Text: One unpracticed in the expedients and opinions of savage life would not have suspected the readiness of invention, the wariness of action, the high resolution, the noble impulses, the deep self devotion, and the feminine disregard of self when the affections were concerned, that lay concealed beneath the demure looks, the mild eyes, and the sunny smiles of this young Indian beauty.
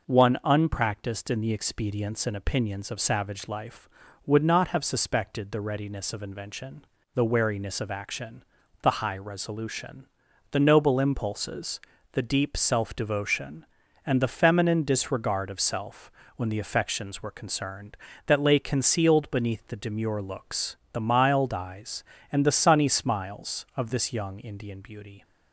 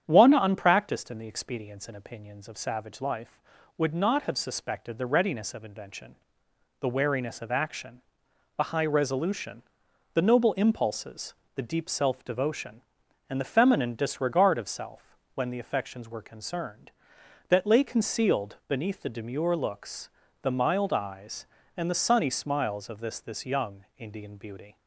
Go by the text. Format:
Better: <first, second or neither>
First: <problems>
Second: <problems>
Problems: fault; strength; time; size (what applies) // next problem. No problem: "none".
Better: first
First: pauses between "self" and "when"; slight; at 16.1 s; 0.24 s long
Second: starts louder than the rest; strong; until 1.0 s; 9 dB // pauses between "self" and "when"; slight; at 15.1 s; 0.16 s long // says "this" twice; at 23.1 s